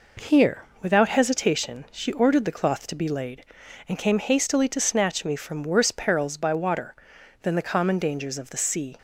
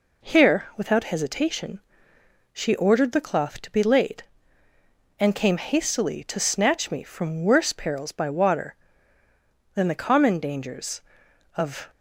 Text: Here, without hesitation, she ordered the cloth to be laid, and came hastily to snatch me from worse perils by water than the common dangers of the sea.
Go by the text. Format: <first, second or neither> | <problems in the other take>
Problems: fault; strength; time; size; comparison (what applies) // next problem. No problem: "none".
first | stops before "the sea"; at 11.9 s